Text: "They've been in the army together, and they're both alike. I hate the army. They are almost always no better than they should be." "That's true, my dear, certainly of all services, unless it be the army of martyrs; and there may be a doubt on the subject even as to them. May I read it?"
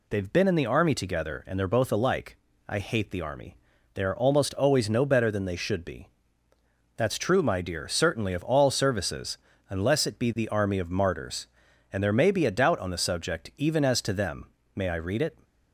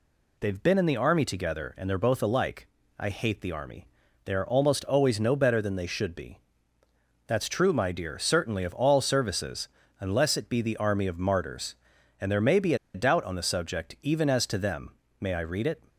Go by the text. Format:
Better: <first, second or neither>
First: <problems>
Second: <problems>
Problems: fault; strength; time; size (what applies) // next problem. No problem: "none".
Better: first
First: none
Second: pauses between "be" and "a"; slight; at 12.7 s; 0.19 s long